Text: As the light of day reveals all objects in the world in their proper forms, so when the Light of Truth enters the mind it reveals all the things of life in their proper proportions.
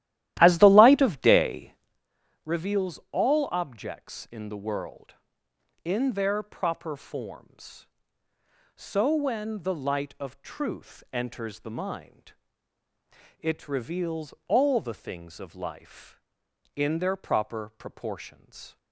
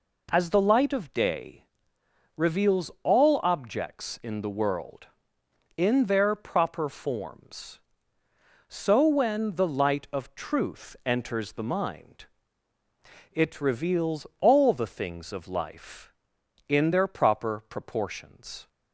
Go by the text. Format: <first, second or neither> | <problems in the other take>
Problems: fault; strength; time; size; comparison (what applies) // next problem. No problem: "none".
second | starts louder than the rest; strong; until 2.0 s; 14 dB // pauses between "day" and "reveals"; noticeable; at 1.7 s; 0.72 s long; noticeable in the second // pauses between "mind" and "it"; at 12.3 s; 1.0 s long; also in the second